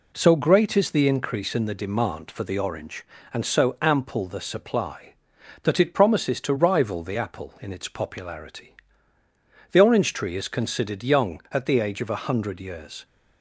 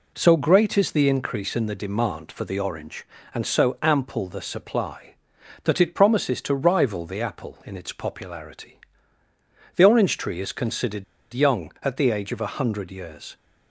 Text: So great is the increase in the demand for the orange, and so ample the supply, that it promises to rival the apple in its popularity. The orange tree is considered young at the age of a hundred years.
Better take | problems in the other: first | pauses between "considered" and "young"; slight; at 11.0 s; 0.29 s long

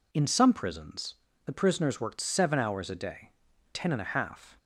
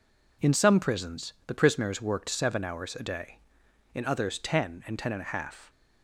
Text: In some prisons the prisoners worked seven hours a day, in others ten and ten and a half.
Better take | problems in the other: second | pauses between "prisons" and "the"; slight; at 1.1 s; 0.30 s long // skips "in others ten and"; at 3.5 s

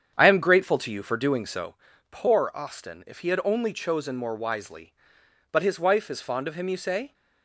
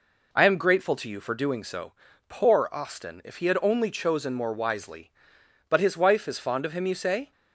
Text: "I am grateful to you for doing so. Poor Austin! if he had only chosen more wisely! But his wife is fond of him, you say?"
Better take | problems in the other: second | starts louder than the rest; strong; until 1.8 s; 8 dB

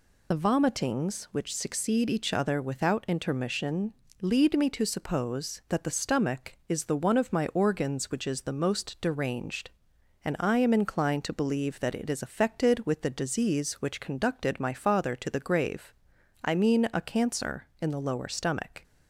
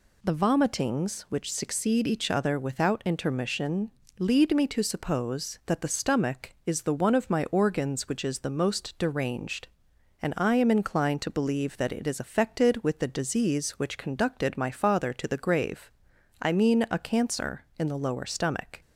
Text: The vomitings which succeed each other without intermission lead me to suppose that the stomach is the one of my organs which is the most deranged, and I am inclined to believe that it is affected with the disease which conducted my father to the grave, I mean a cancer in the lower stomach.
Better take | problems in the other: second | loses the start of "The"; at 0.3 s; 55 ms // pauses between "intermission" and "lead"; slight; at 3.9 s; 0.30 s long; slight in the second

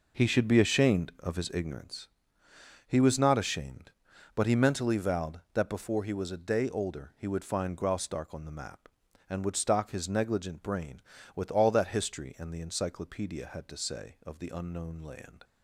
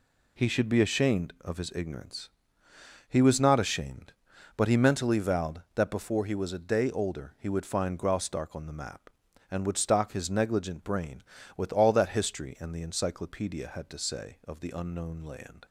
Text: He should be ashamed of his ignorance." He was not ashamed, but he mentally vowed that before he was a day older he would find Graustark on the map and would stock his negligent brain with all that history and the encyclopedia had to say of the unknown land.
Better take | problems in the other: second | starts louder than the rest; noticeable; until 1.9 s; 5 dB

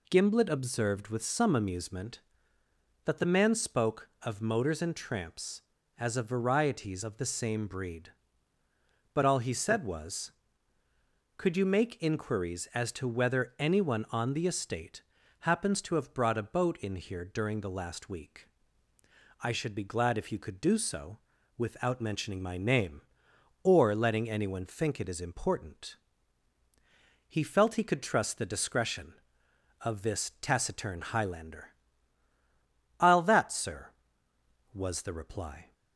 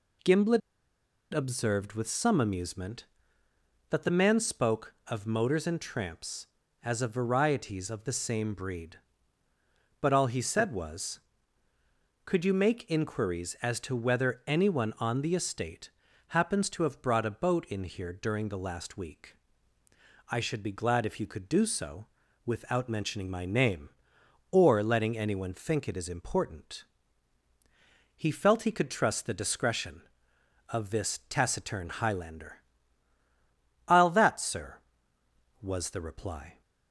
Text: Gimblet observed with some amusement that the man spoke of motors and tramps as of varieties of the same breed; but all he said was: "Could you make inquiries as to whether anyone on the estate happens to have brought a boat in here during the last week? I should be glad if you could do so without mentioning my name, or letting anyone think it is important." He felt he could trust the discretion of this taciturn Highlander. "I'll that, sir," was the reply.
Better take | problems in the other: first | pauses between "Gimblet" and "observed"; noticeable; at 0.6 s; 0.72 s long // pauses between "estate" and "happens"; at 15.9 s; 0.38 s long; also in the first // pauses between "so" and "without"; at 22.0 s; 0.38 s long; also in the first

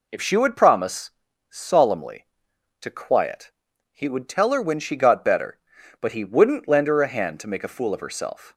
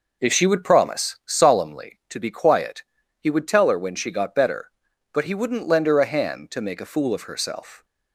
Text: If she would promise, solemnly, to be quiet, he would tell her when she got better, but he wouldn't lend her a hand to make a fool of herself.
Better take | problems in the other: second | skips "be"; at 2.8 s

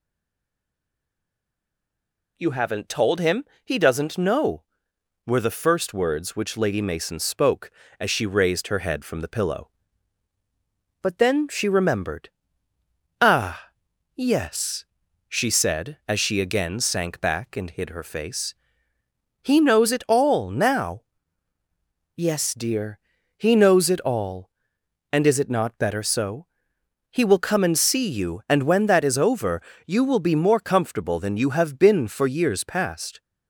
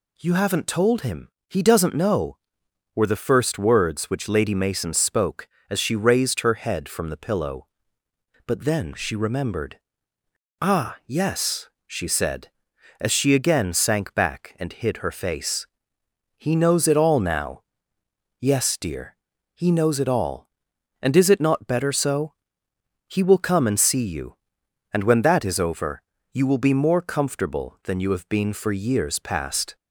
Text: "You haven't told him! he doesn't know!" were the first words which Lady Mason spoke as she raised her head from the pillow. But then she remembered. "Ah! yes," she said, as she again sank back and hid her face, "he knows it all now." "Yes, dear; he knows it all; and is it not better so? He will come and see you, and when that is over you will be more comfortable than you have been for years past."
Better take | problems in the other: second | stays silent before the first word; until 2.3 s; 2.3 s long // pauses between "over" and "you"; slight; at 29.6 s; 0.24 s long; slight in the second

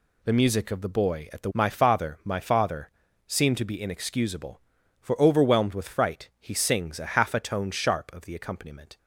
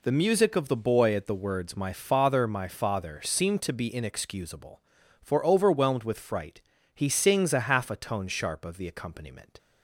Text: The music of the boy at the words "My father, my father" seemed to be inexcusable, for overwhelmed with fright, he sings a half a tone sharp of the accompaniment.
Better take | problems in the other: second | skips "words"; at 1.5 s // pauses between "father" and "seemed"; slight; at 2.8 s; 0.36 s long

